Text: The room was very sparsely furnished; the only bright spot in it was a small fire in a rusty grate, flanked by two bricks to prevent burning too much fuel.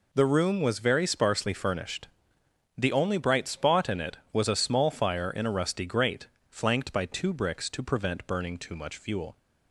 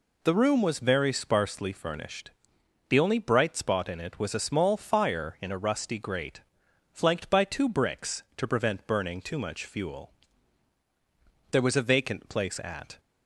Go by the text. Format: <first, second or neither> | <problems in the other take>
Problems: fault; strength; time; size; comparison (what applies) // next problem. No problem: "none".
first | goes on to say "There was a vacant place at"; from 11.5 s on; 1.4 s long